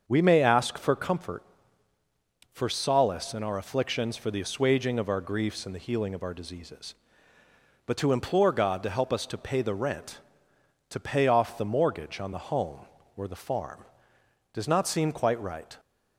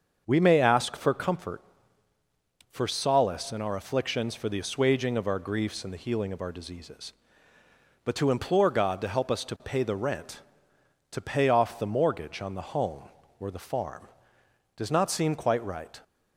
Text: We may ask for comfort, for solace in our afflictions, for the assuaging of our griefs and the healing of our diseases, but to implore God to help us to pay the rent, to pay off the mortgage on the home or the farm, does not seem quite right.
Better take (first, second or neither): neither